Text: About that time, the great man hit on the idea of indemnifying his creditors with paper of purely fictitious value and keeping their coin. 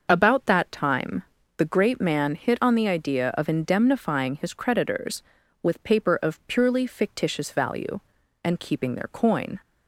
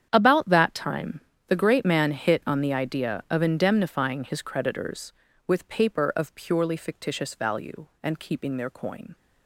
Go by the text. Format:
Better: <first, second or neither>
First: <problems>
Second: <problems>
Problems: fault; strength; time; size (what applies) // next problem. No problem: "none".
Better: first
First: starts louder than the rest; noticeable; until 1.1 s; 6 dB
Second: gets quieter; strong; throughout; 15 dB // starts louder than the rest; strong; until 1.1 s; 9 dB